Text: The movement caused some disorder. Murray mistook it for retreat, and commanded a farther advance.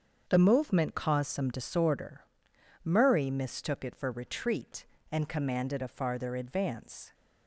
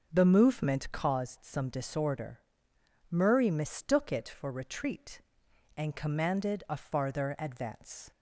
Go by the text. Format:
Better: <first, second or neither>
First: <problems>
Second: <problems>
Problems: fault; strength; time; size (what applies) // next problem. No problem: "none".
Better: neither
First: starts louder than the rest; until 1.3 s; 7 dB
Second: starts louder than the rest; noticeable; until 1.1 s; 6 dB